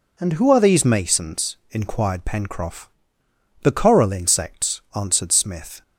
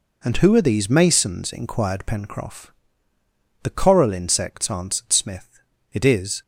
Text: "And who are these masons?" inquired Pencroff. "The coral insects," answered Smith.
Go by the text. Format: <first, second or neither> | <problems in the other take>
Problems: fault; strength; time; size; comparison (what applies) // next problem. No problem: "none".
first | goes on to say "It is"; from 5.9 s on; 0.50 s long